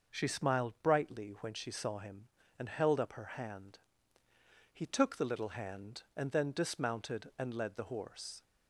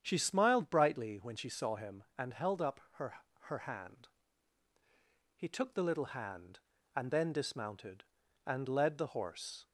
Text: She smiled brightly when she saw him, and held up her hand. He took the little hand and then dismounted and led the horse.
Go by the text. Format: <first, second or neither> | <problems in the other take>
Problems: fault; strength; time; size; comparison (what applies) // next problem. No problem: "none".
first | starts louder than the rest; strong; until 1.0 s; 8.5 dB // says "her" twice; at 3.4 s